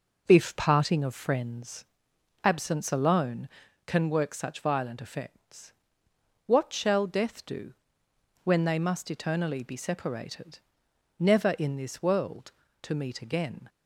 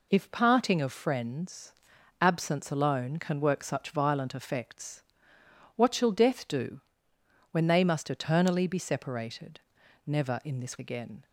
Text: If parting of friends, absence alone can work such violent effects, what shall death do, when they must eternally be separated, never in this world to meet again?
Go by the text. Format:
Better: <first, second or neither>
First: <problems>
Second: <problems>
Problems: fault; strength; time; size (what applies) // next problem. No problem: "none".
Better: first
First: none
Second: skips "world to meet"; at 10.7 s